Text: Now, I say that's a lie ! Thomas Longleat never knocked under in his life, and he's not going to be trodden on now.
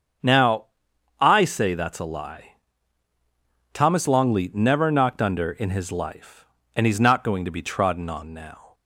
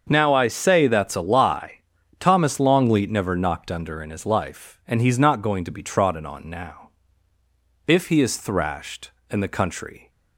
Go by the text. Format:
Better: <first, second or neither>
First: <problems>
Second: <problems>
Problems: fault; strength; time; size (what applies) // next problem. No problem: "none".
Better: first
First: starts louder than the rest; until 1.7 s; 7 dB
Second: starts louder than the rest; until 1.1 s; 6.5 dB // goes on to say "If he is thrashed and the country"; strong; from 7.8 s on; 2.2 s long